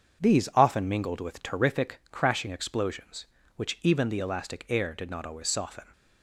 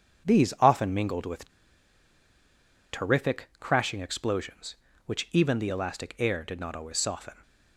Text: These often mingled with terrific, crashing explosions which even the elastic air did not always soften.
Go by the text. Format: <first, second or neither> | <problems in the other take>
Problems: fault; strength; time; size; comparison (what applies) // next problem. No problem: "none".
first | starts louder than the rest; strong; until 1.3 s; 7 dB; strong in the first // pauses between "with" and "terrific"; strong; at 1.4 s; 1.4 s long